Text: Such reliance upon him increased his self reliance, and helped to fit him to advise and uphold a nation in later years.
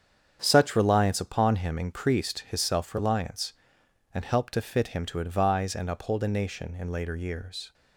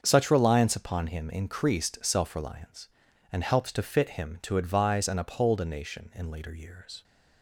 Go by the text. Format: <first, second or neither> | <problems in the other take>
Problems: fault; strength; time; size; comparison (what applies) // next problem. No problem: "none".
first | starts louder than the rest; until 1.0 s; 7 dB; strong in the first // skips "his"; at 2.0 s